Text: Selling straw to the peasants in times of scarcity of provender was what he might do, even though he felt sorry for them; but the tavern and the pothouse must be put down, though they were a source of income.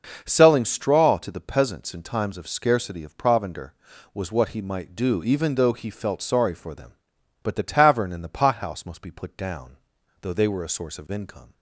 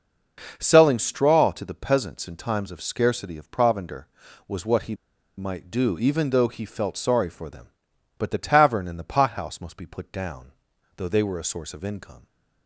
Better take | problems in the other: first | pauses between "he" and "might"; at 4.9 s; 0.42 s long

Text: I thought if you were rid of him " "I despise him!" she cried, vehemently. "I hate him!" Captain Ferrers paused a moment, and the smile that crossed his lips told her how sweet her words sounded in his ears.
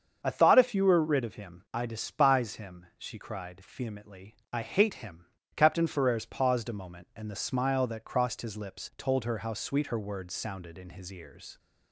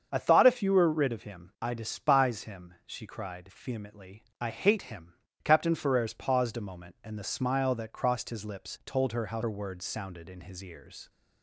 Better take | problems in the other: first | starts louder than the rest; strong; until 1.1 s; 7 dB; strong in the first // skips "sweet"; at 9.4 s

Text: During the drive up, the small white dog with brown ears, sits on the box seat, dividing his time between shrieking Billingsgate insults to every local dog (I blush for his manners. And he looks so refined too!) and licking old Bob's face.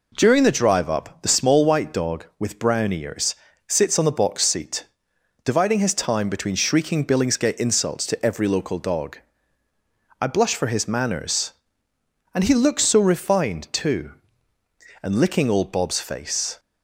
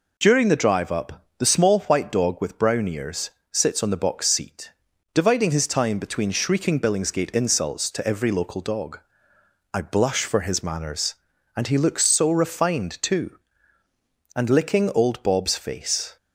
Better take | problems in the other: neither | none

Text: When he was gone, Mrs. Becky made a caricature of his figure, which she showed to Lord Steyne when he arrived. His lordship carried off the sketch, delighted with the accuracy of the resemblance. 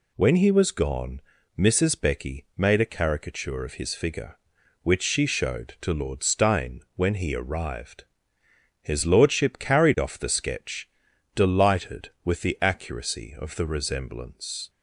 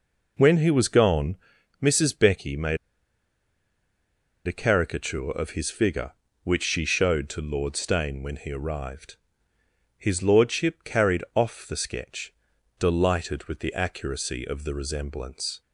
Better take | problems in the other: first | pauses between "made" and "a"; strong; at 2.7 s; 1.6 s long

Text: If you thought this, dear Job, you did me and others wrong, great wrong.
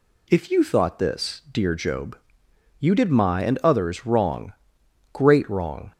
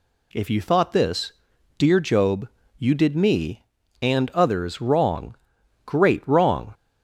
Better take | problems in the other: second | says "my" for "me"; at 3.0 s

